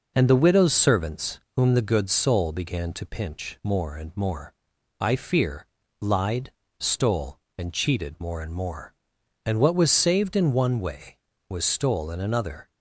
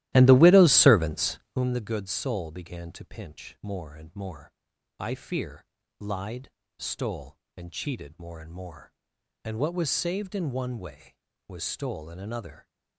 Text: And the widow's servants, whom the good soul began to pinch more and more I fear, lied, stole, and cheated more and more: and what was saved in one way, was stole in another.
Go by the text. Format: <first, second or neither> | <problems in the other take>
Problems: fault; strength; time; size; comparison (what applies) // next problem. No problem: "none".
first | starts louder than the rest; strong; until 1.7 s; 15 dB // pauses between "more" and "I"; noticeable; at 4.5 s; 0.46 s long; noticeable in the first